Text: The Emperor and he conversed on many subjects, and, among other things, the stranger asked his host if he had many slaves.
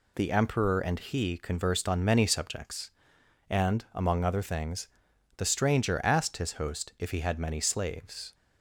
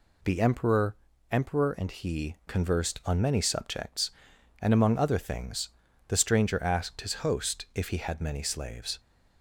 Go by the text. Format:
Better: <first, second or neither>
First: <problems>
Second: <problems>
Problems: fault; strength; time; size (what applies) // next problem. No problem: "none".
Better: first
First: none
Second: says "Emperor" twice; at 1.3 s